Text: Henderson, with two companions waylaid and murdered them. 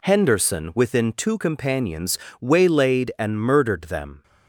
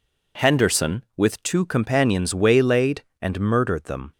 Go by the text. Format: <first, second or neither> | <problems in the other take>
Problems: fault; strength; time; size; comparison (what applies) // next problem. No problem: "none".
second | says "within" for "with"; at 0.7 s // pauses between "companions" and "waylaid"; slight; at 2.1 s; 0.22 s long